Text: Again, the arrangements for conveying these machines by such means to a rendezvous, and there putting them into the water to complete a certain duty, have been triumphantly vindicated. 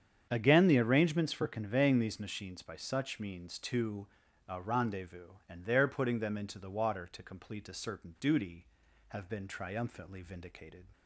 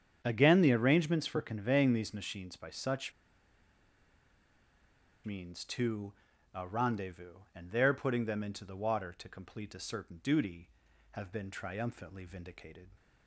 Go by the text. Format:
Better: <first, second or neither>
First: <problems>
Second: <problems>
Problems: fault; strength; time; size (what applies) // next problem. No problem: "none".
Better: first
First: starts louder than the rest; strong; until 1.3 s; 8 dB // pauses between "to" and "a"; at 4.0 s; 0.40 s long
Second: starts louder than the rest; strong; until 1.2 s; 8 dB // pauses between "such" and "means"; strong; at 3.1 s; 2.1 s long // pauses between "to" and "a"; at 6.1 s; 0.40 s long